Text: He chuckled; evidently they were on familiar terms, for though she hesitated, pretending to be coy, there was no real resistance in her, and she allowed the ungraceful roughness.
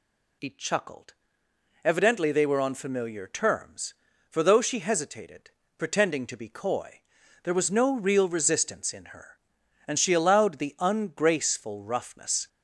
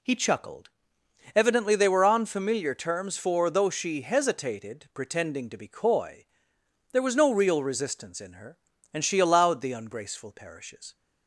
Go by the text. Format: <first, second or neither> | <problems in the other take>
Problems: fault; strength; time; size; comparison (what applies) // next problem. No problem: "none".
first | says "parishes" for "roughness"; at 10.3 s